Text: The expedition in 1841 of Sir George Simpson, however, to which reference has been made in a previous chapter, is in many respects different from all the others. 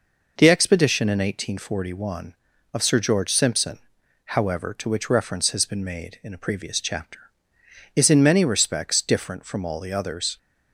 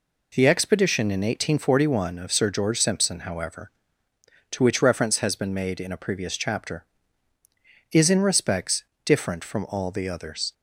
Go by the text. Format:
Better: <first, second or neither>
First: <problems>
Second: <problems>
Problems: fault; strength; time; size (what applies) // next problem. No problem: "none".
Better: first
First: none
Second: skips "many"; at 8.2 s // pauses between "respects" and "different"; slight; at 8.8 s; 0.22 s long